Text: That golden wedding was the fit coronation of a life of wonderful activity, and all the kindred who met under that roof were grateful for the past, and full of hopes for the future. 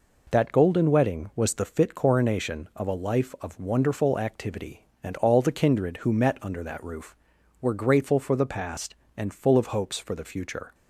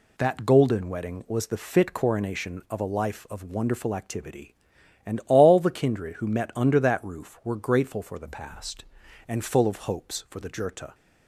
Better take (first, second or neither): first